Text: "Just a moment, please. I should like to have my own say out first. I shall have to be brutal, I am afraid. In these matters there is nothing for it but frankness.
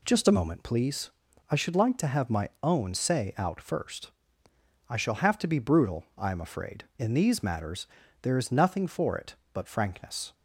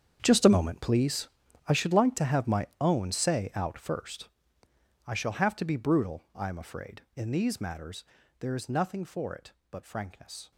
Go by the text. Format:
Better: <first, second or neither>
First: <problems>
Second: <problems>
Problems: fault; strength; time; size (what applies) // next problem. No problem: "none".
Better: first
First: pauses between "matters" and "there"; slight; at 7.8 s; 0.34 s long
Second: gets quieter; strong; throughout; 16 dB // pauses between "matters" and "there"; slight; at 8.0 s; 0.34 s long